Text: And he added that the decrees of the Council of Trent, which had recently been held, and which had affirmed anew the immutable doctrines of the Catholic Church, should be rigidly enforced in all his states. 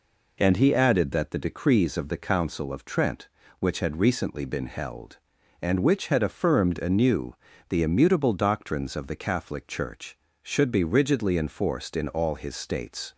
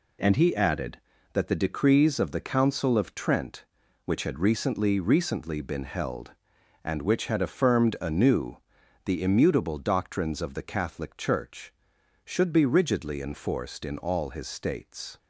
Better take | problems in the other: first | says "recently" twice; at 4.9 s // pauses between "anew" and "the"; noticeable; at 8.5 s; 0.48 s long; slight in the first

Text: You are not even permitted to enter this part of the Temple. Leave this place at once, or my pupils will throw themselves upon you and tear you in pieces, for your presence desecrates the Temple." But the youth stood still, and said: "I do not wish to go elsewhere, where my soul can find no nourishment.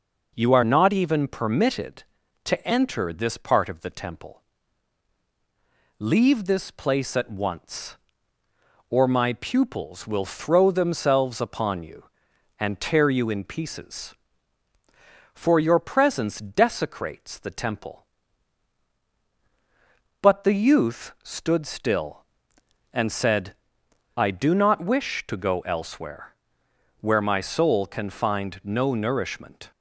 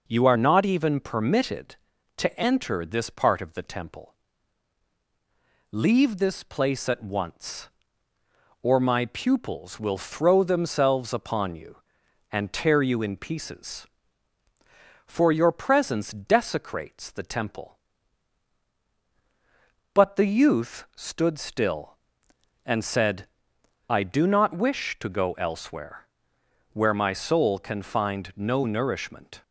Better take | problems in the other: neither | none

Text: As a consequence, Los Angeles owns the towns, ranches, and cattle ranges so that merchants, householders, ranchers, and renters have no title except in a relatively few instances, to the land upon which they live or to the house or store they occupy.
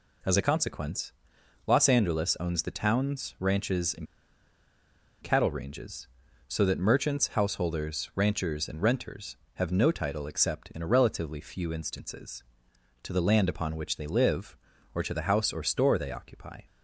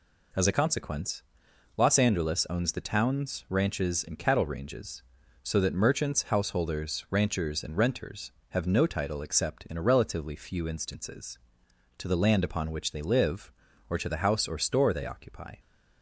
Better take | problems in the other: second | pauses between "and" and "cattle"; at 4.0 s; 1.1 s long

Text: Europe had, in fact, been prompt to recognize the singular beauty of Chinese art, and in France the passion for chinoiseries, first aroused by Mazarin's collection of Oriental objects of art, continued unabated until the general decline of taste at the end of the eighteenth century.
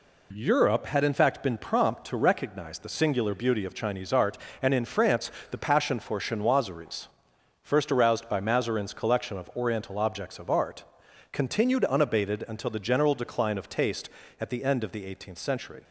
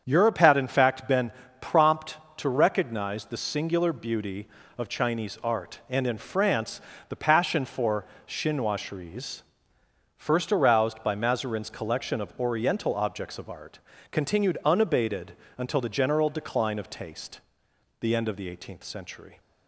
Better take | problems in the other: first | starts louder than the rest; strong; until 1.0 s; 7.5 dB // pauses between "been" and "prompt"; slight; at 1.3 s; 0.28 s long // pauses between "France" and "the"; slight; at 6.8 s; 0.26 s long; slight in the first // pauses between "for" and "chinoiseries"; slight; at 8.0 s; 0.22 s long // pauses between "unabated" and "until"; slight; at 15.3 s; 0.24 s long // skips "at"; at 17.7 s

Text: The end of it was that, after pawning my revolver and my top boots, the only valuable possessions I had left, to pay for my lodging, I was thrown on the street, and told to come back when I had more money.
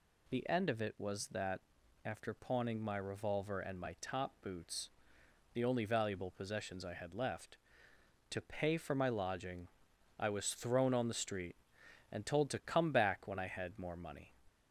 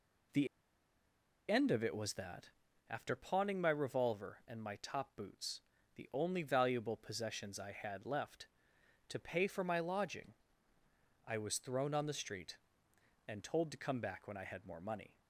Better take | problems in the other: first | pauses between "The" and "end"; at 0.4 s; 1.0 s long

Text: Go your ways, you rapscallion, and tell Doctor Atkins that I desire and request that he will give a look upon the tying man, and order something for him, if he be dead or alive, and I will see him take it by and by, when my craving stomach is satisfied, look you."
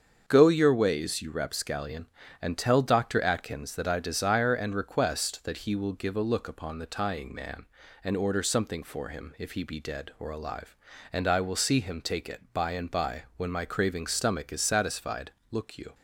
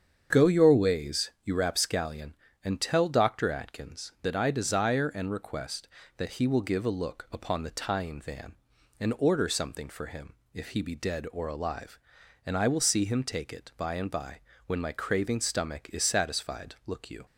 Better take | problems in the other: first | starts louder than the rest; strong; until 1.4 s; 7.5 dB; also in the first // says "van" for "man"; at 8.2 s

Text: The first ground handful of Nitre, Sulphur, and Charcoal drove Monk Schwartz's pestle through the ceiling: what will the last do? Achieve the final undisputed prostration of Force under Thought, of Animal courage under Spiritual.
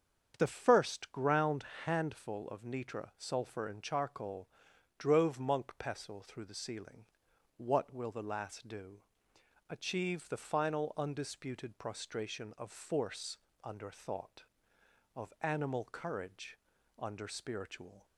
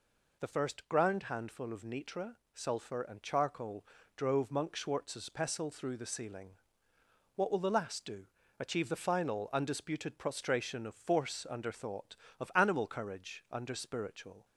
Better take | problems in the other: second | starts louder than the rest; strong; until 1.3 s; 7.5 dB // pauses between "ground" and "handful"; slight; at 1.6 s; 0.22 s long // pauses between "Charcoal" and "drove"; noticeable; at 4.4 s; 0.48 s long; slight in the second // skips "Schwartz's"; at 5.7 s // pauses between "Force" and "under"; slight; at 13.3 s; 0.26 s long // pauses between "courage" and "under"; at 16.5 s; 0.42 s long

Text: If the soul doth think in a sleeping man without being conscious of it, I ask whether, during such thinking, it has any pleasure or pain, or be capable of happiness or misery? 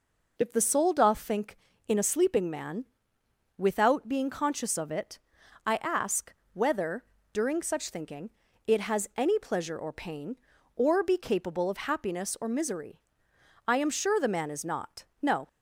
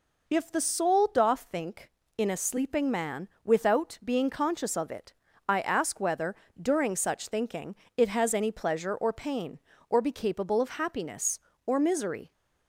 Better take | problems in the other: second | pauses between "man" and "without"; noticeable; at 2.8 s; 0.72 s long; slight in the second // pauses between "ask" and "whether"; slight; at 6.3 s; 0.20 s long // goes on to say "I am sure the man is not no"; strong; from 13.6 s on; 1.8 s long

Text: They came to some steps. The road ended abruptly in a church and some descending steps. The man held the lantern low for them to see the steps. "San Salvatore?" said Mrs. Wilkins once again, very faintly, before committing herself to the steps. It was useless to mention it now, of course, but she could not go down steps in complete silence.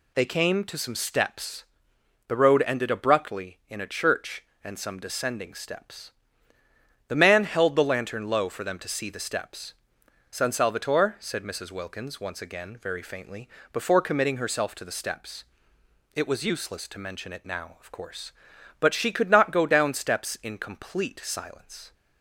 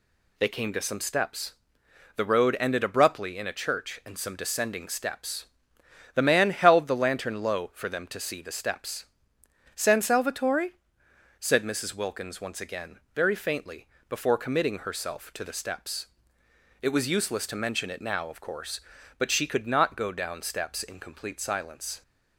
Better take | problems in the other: neither | none

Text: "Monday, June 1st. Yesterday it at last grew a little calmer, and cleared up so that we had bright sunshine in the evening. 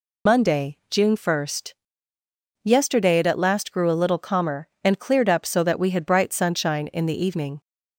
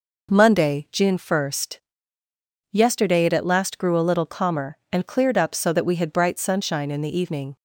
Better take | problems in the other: second | loses the start of "Monday"; at 0.2 s; 70 ms

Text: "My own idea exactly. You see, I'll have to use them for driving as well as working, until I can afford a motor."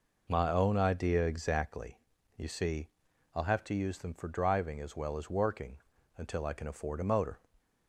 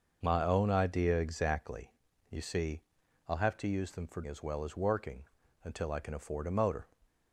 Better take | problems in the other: first | skips "driving"; at 4.2 s

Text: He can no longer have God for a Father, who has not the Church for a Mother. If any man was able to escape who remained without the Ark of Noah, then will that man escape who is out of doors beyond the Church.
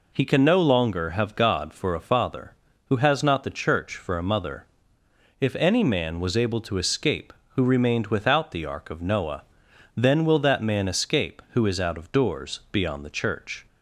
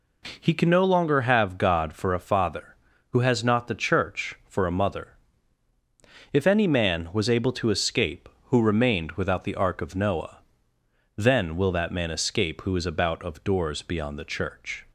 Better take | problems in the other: first | says "about" for "out"; at 12.8 s

